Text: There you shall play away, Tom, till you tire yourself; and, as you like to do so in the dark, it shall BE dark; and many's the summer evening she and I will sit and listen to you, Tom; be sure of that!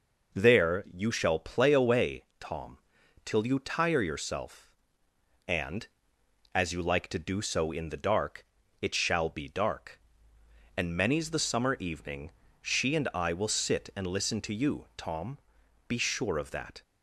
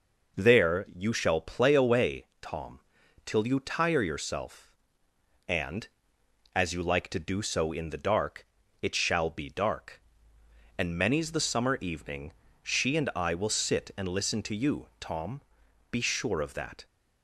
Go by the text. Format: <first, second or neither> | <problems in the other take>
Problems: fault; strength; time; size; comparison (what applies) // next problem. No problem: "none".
neither | pauses between "evening" and "she"; slight; the same in both